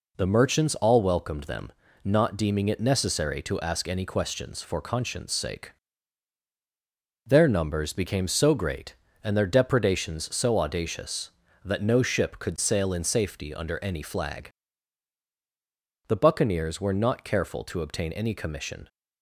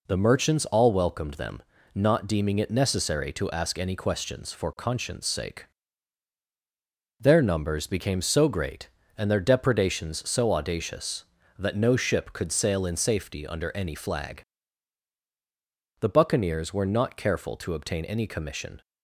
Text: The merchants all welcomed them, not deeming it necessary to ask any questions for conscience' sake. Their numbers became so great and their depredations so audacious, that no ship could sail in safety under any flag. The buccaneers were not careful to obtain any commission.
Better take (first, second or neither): neither